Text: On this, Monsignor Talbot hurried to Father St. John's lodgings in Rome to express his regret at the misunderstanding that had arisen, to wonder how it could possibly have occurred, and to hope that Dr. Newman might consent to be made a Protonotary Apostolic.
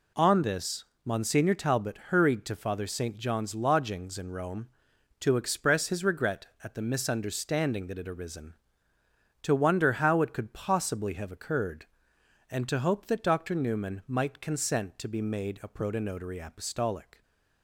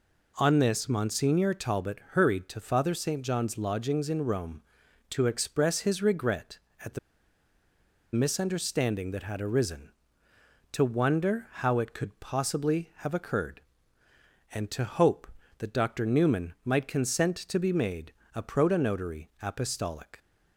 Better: first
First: none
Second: pauses between "the" and "misunderstanding"; at 6.9 s; 1.1 s long // pauses between "made" and "a"; slight; at 18.1 s; 0.22 s long

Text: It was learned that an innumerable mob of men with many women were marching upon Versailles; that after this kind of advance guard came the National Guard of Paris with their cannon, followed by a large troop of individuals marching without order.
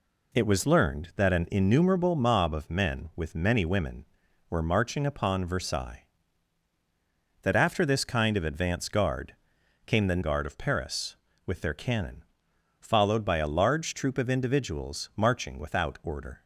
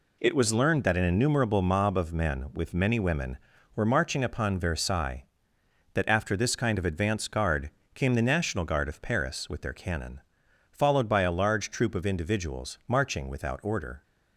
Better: second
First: pauses between "guard" and "came"; noticeable; at 9.3 s; 0.50 s long // skips "National"; at 10.2 s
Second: pauses between "guard" and "came"; slight; at 7.7 s; 0.24 s long

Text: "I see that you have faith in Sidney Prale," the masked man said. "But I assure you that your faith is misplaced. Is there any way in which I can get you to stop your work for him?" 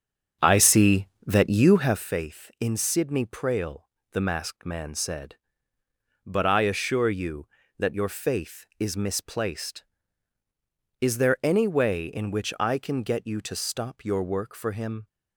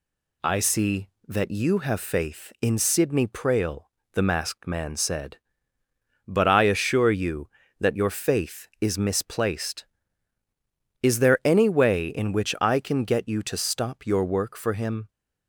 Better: second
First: starts louder than the rest; strong; until 2.1 s; 7 dB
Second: none

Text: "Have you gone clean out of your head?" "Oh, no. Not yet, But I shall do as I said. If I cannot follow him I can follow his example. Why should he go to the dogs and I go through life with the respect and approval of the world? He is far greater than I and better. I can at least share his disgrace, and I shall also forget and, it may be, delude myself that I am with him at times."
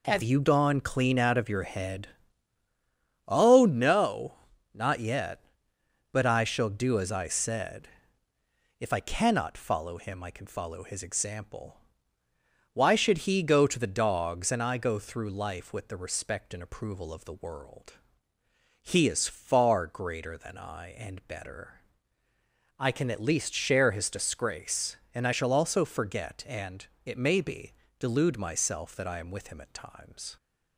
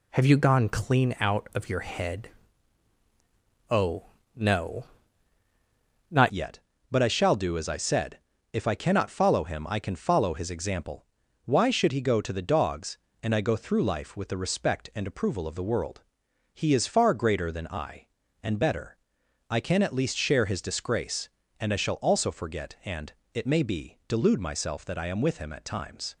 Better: first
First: none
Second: changes voice at "yet"; from 6.3 s on; 19.8 s long

